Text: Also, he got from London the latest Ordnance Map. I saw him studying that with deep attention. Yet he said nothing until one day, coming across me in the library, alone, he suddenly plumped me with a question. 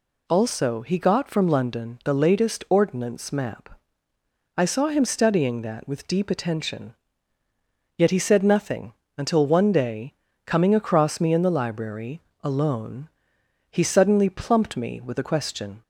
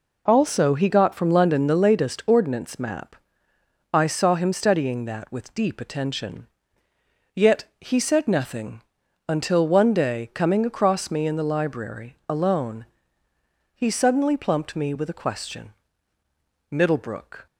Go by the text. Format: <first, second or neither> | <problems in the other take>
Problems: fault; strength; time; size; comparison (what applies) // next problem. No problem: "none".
first | pauses between "nothing" and "until"; noticeable; at 8.8 s; 0.48 s long; slight in the first // goes on to say "Middlebrook"; noticeable; from 16.7 s on; 0.76 s long